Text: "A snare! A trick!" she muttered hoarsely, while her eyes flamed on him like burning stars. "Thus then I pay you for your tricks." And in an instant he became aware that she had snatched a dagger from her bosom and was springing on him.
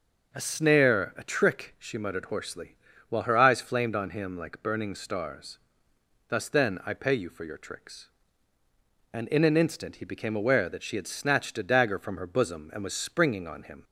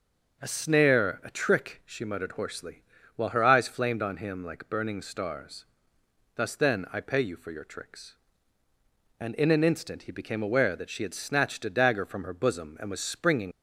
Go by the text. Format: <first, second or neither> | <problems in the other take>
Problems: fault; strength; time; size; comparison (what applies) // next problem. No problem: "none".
first | stops before "on him"; at 13.5 s